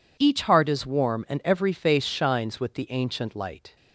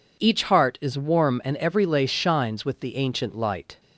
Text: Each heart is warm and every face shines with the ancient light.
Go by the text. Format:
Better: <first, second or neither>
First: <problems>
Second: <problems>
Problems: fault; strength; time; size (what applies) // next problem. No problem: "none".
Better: first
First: none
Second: says "lace" for "face"; at 1.8 s